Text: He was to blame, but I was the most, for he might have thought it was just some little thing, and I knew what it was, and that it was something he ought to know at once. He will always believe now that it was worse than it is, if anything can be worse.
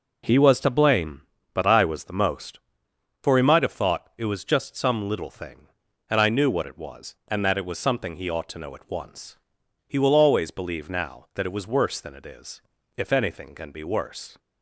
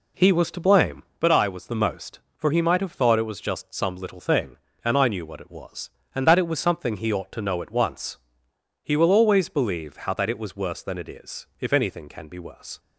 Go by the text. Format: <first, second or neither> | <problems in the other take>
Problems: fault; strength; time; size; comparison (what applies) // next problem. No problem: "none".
first | says "how" for "now"; at 9.9 s